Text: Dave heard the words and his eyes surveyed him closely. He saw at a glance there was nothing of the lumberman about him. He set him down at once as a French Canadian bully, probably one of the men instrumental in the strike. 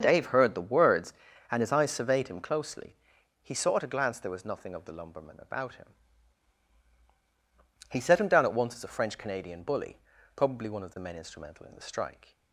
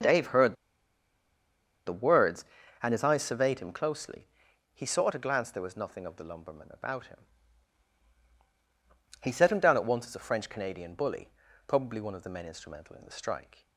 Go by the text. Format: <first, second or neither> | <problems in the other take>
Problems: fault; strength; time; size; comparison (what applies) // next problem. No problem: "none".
first | starts louder than the rest; until 2.3 s; 7 dB; also in the first // pauses between "heard" and "the"; strong; at 0.5 s; 1.3 s long